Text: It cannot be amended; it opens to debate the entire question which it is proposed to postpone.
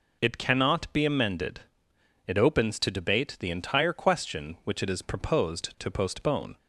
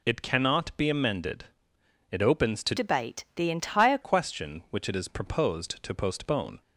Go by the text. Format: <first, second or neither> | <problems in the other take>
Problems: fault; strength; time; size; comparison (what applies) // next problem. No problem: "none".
first | changes voice from "debate" to "entire"; from 2.7 to 3.9 s; 1.2 s long